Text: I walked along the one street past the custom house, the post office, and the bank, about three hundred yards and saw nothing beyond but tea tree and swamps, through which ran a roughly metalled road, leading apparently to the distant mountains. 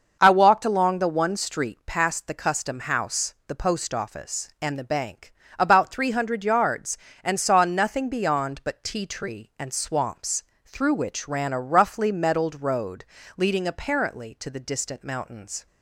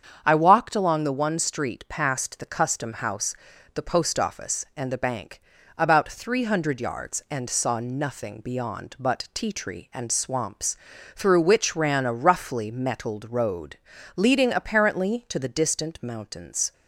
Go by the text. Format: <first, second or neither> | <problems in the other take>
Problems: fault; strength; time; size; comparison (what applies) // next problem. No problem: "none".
neither | starts louder than the rest; the same in both